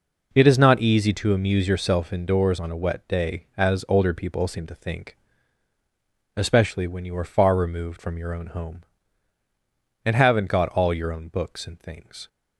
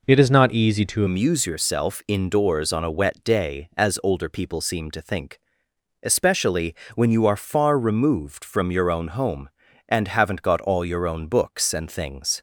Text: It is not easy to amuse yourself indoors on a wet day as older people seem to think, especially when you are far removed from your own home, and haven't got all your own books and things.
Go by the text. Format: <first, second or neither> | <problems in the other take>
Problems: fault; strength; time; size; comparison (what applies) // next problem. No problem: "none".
first | changes voice at "amuse"; from 1.0 s on; 11.4 s long // pauses between "especially" and "when"; slight; at 6.7 s; 0.20 s long